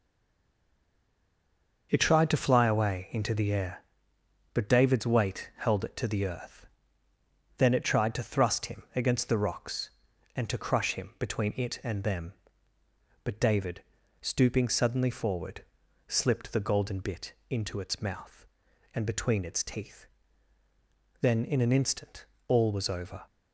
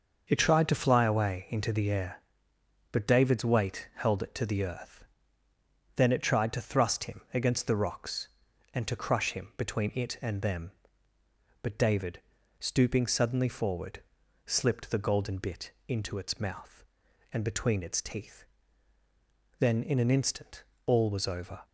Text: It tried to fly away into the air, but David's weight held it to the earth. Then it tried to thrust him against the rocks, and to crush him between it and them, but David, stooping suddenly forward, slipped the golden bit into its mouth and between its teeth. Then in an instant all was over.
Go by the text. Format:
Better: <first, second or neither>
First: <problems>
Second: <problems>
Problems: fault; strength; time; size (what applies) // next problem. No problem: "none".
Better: second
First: stays silent before the first word; noticeable; until 1.9 s; 1.9 s long // starts louder than the rest; noticeable; until 2.9 s; 6 dB // pauses between "bit" and "into"; slight; at 17.3 s; 0.18 s long // pauses between "instant" and "all"; slight; at 22.2 s; 0.22 s long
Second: starts louder than the rest; until 1.2 s; 6 dB // pauses between "bit" and "into"; slight; at 15.7 s; 0.18 s long // pauses between "instant" and "all"; slight; at 20.6 s; 0.22 s long